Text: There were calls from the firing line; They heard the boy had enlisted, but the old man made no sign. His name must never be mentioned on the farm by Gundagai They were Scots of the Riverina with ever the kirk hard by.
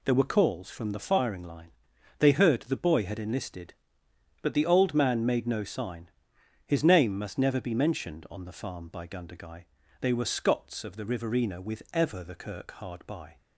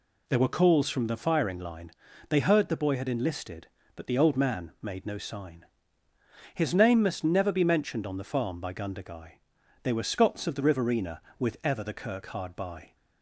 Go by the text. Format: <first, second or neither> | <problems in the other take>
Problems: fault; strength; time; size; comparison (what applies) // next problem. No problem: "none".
neither | pauses between "Gundagai" and "They"; the same in both